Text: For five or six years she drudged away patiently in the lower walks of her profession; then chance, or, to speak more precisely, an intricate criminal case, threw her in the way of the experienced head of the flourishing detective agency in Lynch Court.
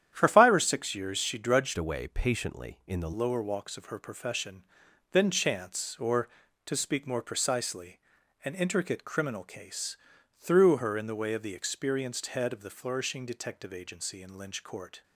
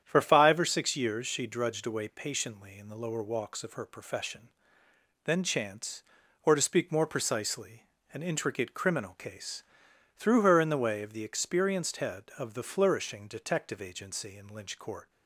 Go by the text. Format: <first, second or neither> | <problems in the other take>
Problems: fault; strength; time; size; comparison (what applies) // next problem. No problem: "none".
second | starts louder than the rest; strong; until 1.1 s; 10 dB; strong in the second // changes voice from "away" to "the"; from 1.7 to 3.1 s; 1.4 s long